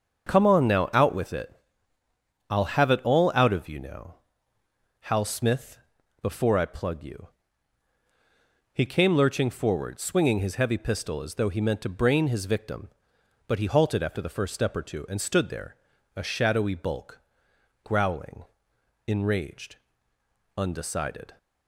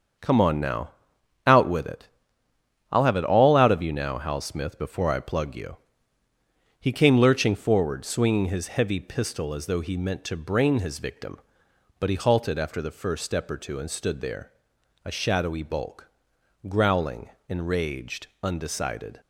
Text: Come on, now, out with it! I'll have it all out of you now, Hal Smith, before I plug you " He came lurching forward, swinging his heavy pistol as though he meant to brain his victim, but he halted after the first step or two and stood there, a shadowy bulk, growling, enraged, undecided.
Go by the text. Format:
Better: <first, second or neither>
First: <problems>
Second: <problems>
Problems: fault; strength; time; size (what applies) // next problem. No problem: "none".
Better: neither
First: starts louder than the rest; strong; until 1.3 s; 7.5 dB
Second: starts louder than the rest; strong; until 1.7 s; 7 dB